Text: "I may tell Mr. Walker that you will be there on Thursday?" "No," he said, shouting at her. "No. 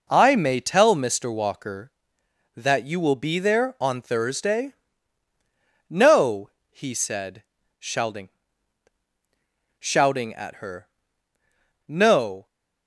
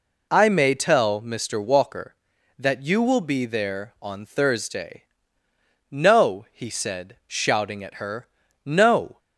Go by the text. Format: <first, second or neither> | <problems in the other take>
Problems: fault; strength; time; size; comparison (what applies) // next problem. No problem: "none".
second | says "shouting" twice; at 9.7 s